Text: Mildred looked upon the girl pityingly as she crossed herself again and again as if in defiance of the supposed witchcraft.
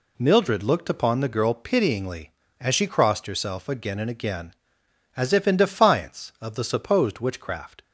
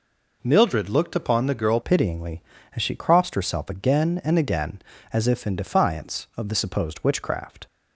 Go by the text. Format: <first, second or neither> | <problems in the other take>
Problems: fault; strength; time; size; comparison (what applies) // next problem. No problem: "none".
first | changes voice at "pityingly"; from 1.8 s on; 5.8 s long